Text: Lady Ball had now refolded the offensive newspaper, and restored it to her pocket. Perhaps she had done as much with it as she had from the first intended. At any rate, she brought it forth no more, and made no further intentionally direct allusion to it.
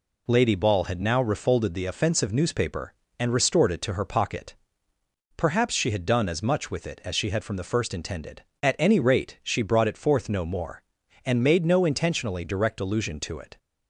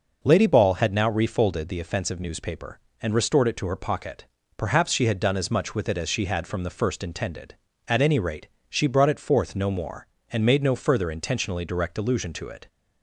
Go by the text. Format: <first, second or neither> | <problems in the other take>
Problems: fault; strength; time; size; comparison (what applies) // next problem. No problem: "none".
second | skips "further"; at 11.8 s